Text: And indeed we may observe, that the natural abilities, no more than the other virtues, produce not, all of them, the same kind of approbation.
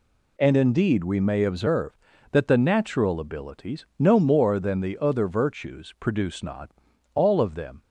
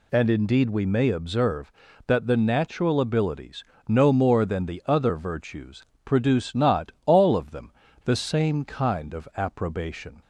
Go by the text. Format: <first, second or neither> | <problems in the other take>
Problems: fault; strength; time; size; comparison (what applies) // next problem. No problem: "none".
second | stops before "the same kind of approbation"; at 7.8 s